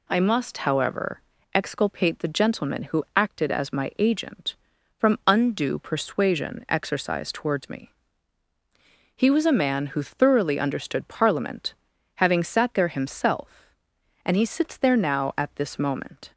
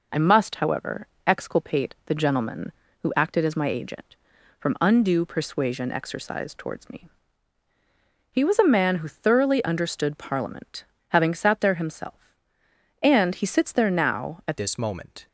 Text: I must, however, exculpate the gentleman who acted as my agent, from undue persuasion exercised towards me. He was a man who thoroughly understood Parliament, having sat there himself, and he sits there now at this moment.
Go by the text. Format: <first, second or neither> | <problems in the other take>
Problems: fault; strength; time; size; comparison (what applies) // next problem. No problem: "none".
first | changes voice at "this"; from 14.5 s on; 0.7 s long